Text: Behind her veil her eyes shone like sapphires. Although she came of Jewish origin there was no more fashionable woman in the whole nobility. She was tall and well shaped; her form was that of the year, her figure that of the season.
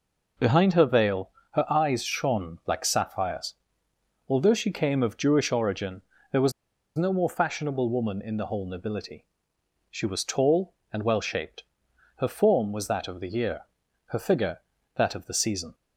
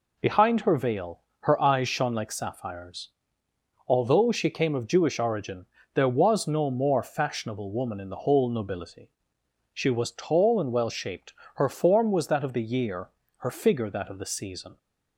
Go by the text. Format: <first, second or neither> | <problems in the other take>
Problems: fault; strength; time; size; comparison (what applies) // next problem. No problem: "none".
second | pauses between "veil" and "her"; slight; at 1.3 s; 0.22 s long; slight in the second // pauses between "origin" and "there"; slight; at 6.0 s; 0.28 s long; slight in the second // pauses between "was" and "no"; at 6.5 s; 0.44 s long